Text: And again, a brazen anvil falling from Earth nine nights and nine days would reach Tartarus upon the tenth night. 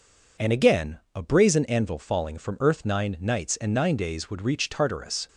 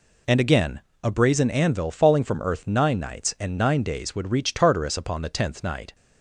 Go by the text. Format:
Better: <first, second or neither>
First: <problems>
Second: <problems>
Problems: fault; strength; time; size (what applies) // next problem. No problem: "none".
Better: second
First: stops before "upon the tenth night"; at 5.2 s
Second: none